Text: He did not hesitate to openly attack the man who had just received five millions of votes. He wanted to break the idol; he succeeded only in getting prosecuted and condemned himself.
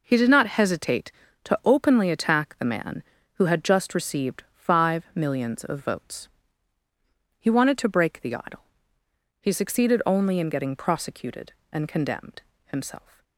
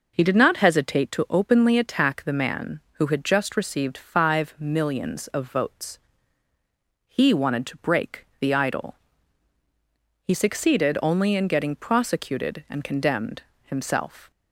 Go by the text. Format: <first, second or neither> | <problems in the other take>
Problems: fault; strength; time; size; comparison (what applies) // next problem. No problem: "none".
neither | pauses between "condemned" and "himself"; slight; the same in both